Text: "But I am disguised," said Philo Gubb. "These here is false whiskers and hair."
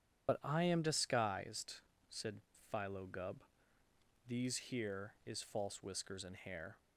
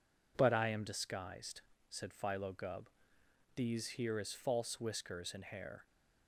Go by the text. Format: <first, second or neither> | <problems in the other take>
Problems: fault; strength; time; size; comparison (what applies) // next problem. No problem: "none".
second | loses the start of "But"; at 0.2 s; 40 ms // pauses between "said" and "Philo"; slight; at 2.4 s; 0.28 s long